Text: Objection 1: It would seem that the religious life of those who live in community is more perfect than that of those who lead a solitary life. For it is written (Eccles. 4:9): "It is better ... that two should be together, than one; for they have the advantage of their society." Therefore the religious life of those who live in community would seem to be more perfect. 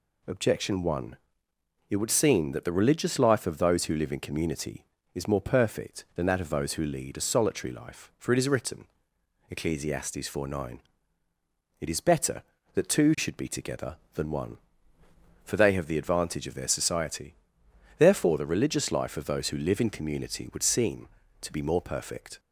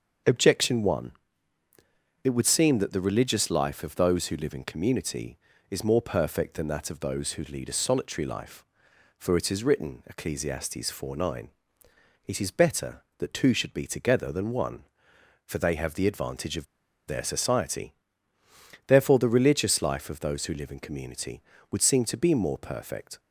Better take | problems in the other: first | starts louder than the rest; until 2.3 s; 6.5 dB // pauses between "of" and "their"; at 16.6 s; 0.41 s long

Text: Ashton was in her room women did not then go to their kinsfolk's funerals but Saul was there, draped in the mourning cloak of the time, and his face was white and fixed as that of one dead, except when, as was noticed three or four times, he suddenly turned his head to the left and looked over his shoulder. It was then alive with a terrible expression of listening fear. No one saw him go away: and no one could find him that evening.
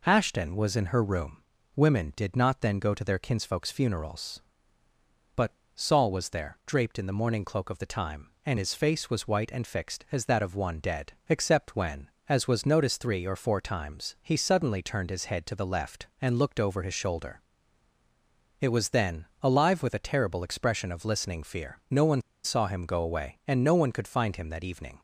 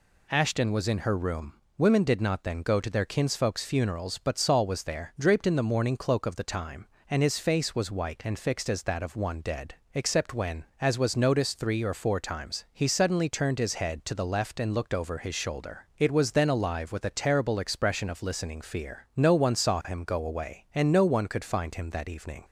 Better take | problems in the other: second | pauses between "room" and "women"; slight; at 1.4 s; 0.34 s long; slight in the second // pauses between "but" and "Saul"; slight; at 5.5 s; 0.22 s long // pauses between "then" and "alive"; slight; at 19.2 s; 0.16 s long // pauses between "one" and "saw"; slight; at 22.2 s; 0.22 s long

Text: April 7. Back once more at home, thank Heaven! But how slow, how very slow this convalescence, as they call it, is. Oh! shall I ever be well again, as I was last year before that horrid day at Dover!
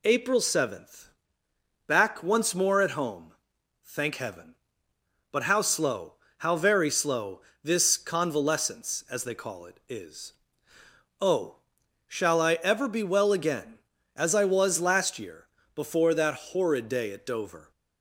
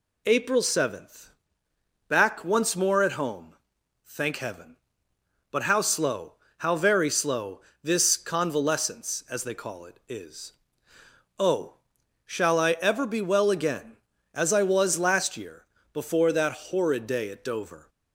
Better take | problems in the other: neither | pauses between "slow" and "this"; slight; the same in both // pauses between "year" and "before"; slight; the same in both

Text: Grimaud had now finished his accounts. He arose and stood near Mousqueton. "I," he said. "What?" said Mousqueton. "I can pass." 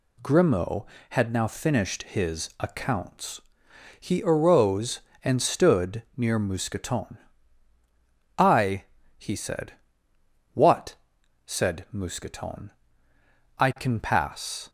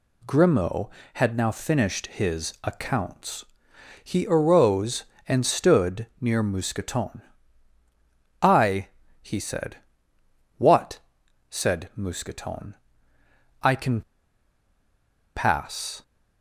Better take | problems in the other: first | pauses between "can" and "pass"; strong; at 14.0 s; 1.3 s long

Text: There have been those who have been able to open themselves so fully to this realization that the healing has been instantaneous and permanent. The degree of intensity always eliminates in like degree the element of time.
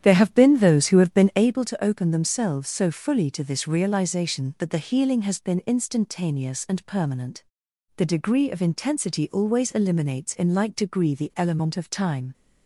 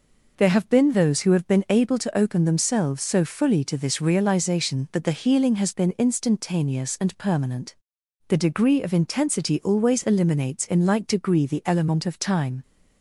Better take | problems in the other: second | starts louder than the rest; strong; until 1.5 s; 10 dB

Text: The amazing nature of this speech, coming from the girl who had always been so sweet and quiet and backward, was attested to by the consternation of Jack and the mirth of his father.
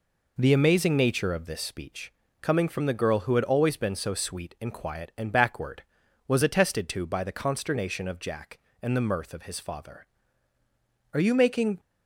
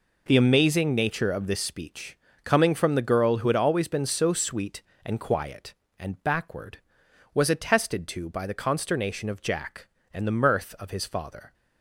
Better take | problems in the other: second | goes on to say "Are you making"; noticeable; from 11.1 s on; 0.66 s long

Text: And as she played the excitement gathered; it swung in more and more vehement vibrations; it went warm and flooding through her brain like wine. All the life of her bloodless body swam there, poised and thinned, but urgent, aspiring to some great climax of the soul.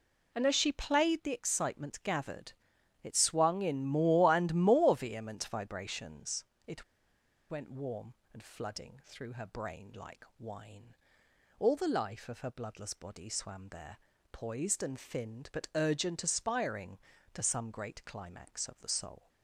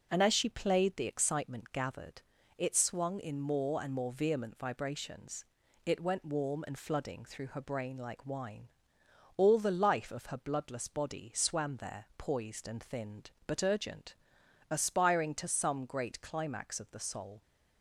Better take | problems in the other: second | pauses between "it" and "went"; noticeable; at 6.8 s; 0.66 s long

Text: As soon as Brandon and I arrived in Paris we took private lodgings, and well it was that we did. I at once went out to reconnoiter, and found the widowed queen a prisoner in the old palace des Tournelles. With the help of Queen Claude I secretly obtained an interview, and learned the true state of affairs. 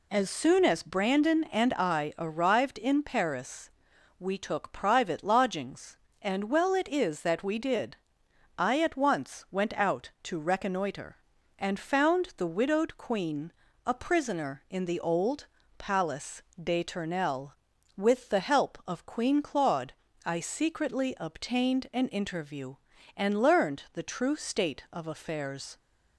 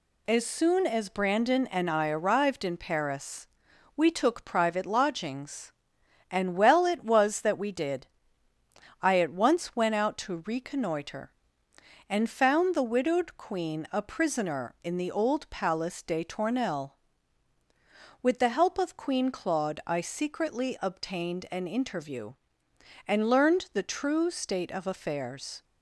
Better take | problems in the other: second | pauses between "Paris" and "we"; noticeable; at 3.6 s; 0.48 s long; noticeable in the second // says "is" for "was"; at 6.8 s // pauses between "queen" and "a"; slight; at 13.5 s; 0.34 s long // pauses between "old" and "palace"; slight; at 15.4 s; 0.32 s long // pauses between "palace" and "des"; slight; at 16.4 s; 0.20 s long // pauses between "Claude" and "I"; slight; at 19.9 s; 0.32 s long

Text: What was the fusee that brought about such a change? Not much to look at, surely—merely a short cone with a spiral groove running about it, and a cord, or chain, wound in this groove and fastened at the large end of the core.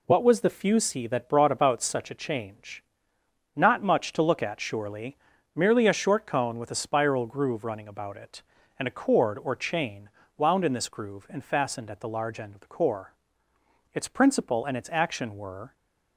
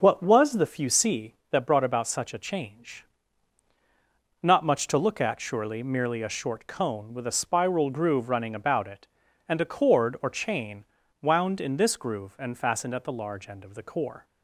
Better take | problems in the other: second | goes on to say "Its principle and its action were"; strong; from 13.9 s on; 1.8 s long

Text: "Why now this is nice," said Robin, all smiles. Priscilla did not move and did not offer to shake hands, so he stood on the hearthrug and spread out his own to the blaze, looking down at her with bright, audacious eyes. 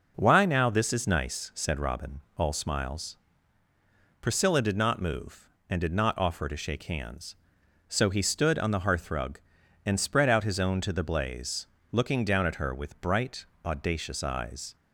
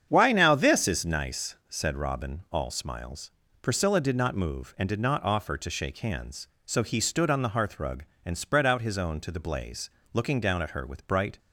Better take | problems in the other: first | starts louder than the rest; strong; until 1.1 s; 8 dB // stops before "audacious eyes"; at 11.3 s

